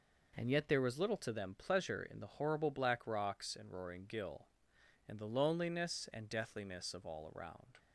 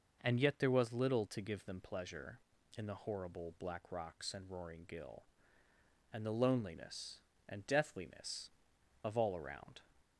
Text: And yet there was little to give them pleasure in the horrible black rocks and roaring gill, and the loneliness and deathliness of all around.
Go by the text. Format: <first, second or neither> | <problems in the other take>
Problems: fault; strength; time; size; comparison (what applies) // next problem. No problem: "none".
second | skips "give"; at 1.3 s